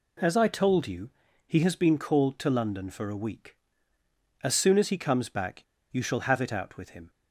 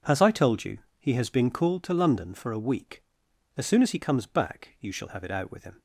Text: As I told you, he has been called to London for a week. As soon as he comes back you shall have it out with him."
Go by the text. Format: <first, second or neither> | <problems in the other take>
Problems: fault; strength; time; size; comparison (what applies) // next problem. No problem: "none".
second | pauses between "back" and "you"; slight; at 5.6 s; 0.28 s long